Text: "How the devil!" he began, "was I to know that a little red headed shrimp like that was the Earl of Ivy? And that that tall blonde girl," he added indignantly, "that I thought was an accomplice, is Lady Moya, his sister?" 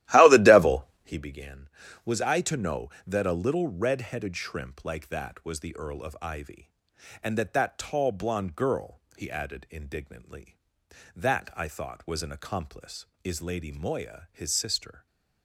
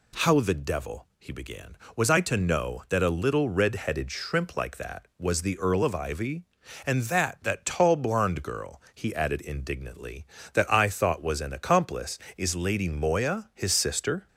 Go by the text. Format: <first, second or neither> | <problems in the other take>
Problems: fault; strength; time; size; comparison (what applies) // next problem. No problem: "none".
second | starts louder than the rest; strong; until 1.2 s; 14.5 dB // stays silent after the last word; slight; from 14.9 s on; 0.5 s long